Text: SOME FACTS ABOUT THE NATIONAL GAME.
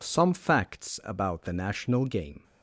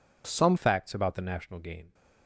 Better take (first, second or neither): first